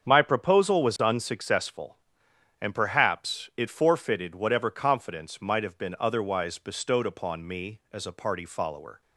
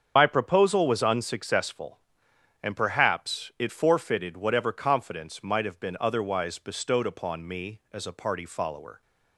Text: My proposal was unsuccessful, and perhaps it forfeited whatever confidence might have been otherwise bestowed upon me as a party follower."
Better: first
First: starts louder than the rest; strong; until 1.0 s; 7.5 dB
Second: loses the start of "My"; at 0.1 s; 70 ms // starts louder than the rest; strong; until 1.1 s; 7.5 dB

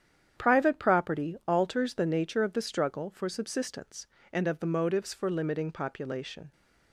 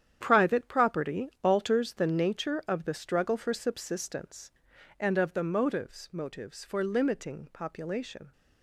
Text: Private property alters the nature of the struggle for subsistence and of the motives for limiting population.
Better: first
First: starts louder than the rest; strong; until 1.5 s; 9 dB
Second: starts louder than the rest; strong; until 1.2 s; 9.5 dB // says "motives" twice; at 6.1 s

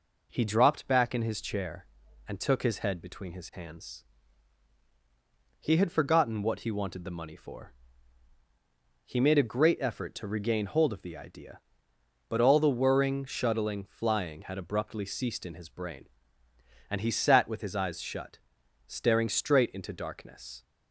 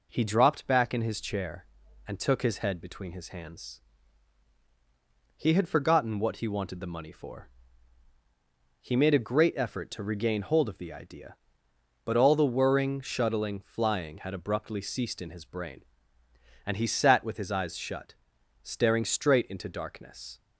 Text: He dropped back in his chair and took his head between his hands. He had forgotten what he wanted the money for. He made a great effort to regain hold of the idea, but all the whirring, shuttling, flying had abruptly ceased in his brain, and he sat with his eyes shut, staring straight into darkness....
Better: neither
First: none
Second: none

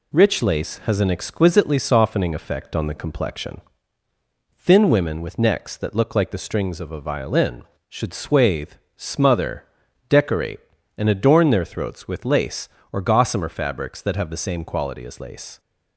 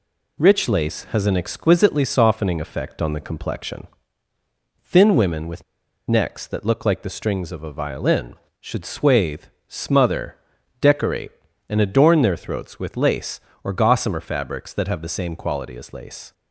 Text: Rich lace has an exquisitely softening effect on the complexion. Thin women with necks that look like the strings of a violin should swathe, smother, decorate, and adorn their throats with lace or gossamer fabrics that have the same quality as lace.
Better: first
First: none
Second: pauses between "with" and "necks"; at 5.6 s; 0.45 s long

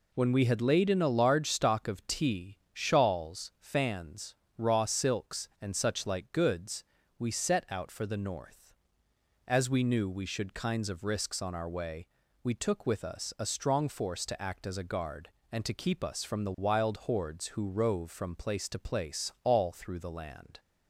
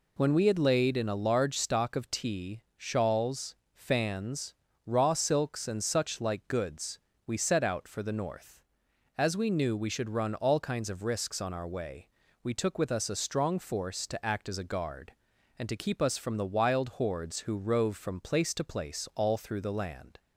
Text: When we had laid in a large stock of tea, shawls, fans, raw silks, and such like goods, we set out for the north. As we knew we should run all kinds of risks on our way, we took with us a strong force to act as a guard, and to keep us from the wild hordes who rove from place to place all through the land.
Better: second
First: skips "run all"; at 10.5 s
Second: none

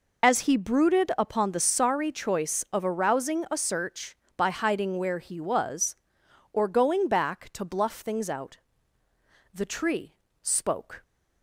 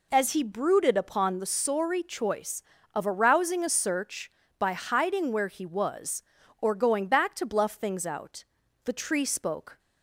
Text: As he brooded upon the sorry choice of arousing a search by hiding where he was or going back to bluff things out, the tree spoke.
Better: second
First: loses the start of "As"; at 0.2 s; 50 ms // pauses between "tree" and "spoke"; slight; at 10.1 s; 0.28 s long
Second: none

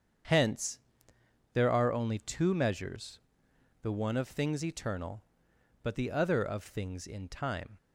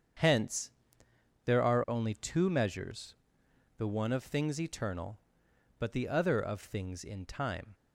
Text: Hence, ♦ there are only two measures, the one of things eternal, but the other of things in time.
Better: neither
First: starts louder than the rest; strong; until 2.0 s; 7.5 dB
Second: starts louder than the rest; strong; until 1.9 s; 7.5 dB

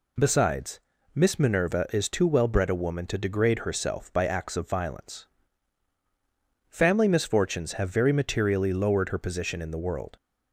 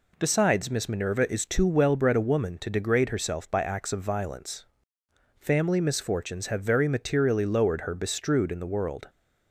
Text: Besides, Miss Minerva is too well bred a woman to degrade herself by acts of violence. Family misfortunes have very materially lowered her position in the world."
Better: first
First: none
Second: says "bestrewed" for "position"; at 7.9 s

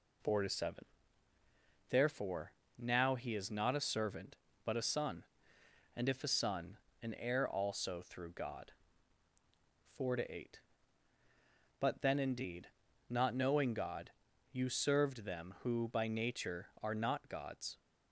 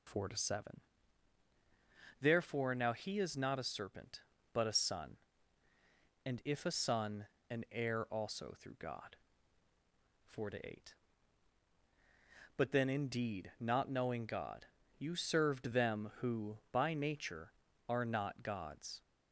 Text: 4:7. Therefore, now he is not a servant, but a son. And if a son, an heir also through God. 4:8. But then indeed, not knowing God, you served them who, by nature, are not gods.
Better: first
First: none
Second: says "serpent" for "servant"; at 3.6 s

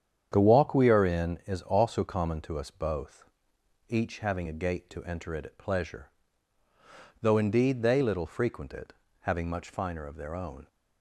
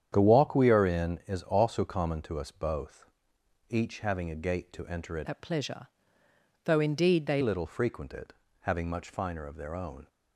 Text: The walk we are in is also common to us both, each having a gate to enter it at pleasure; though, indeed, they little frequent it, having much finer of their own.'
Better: first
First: starts louder than the rest; strong; until 1.3 s; 8.5 dB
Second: starts louder than the rest; strong; until 1.1 s; 9 dB // changes voice from "at" to "they"; from 5.2 to 7.4 s; 2.2 s long

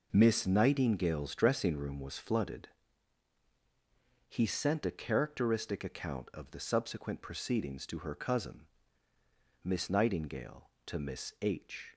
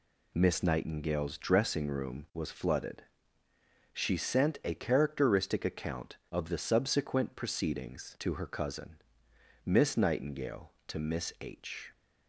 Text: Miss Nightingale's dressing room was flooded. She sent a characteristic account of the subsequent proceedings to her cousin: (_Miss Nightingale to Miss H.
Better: second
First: says "He" for "She"; at 4.2 s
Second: none

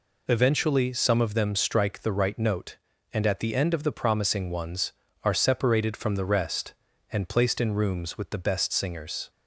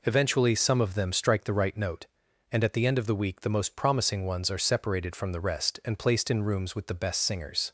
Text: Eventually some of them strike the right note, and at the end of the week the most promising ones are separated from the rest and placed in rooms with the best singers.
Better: second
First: skips "week the most"; at 3.9 s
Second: none

